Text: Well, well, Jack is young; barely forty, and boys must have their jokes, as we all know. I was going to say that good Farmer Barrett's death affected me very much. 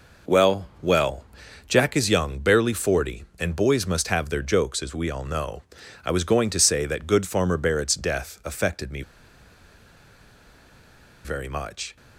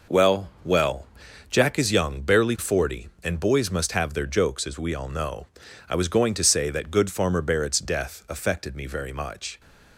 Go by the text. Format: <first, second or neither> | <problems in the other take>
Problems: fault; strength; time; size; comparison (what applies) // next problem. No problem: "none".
second | pauses between "me" and "very"; strong; at 9.0 s; 2.2 s long